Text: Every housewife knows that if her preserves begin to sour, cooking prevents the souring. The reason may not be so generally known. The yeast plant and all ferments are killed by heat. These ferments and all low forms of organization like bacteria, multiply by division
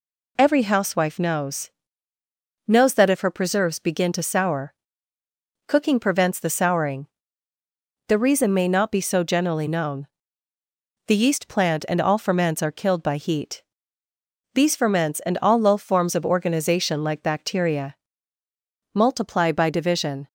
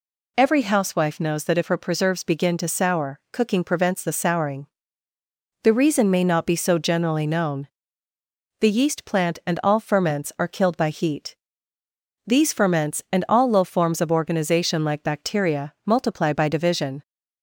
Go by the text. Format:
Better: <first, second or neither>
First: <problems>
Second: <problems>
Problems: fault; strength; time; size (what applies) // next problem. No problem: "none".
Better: second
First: says "knows" twice; at 2.6 s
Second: none